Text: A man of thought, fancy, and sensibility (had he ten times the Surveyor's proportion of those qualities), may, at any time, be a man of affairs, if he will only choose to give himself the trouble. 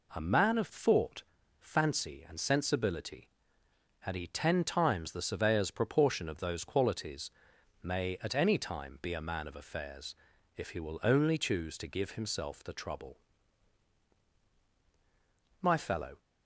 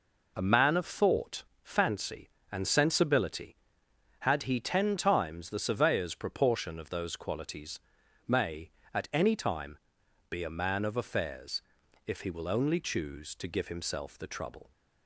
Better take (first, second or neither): second